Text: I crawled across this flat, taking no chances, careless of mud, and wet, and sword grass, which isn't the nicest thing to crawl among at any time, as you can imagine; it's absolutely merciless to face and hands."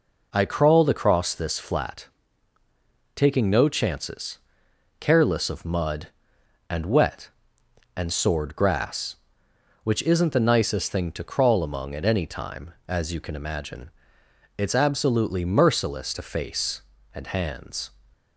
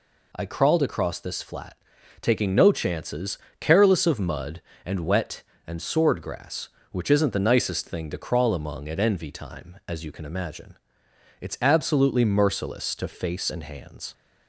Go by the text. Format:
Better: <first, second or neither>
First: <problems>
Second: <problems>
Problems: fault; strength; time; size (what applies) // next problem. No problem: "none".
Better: first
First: none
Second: says "envy" for "any"; at 8.9 s